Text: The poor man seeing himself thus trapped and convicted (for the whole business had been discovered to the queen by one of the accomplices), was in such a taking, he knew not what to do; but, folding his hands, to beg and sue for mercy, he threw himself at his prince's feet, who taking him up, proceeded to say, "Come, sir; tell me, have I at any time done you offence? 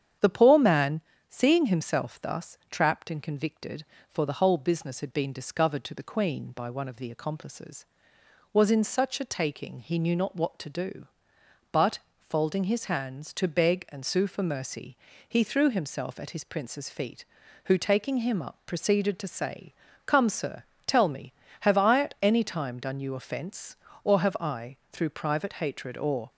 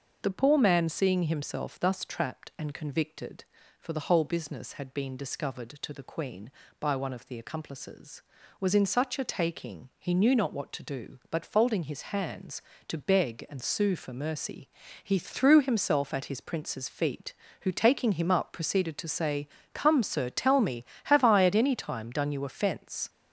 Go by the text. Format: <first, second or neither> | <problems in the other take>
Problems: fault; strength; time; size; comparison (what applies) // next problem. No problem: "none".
second | starts louder than the rest; strong; until 1.5 s; 9 dB; also in the second // pauses between "man" and "seeing"; slight; at 1.0 s; 0.28 s long // goes on to say "or have I through private hatred or"; strong; from 24.0 s on; 2.2 s long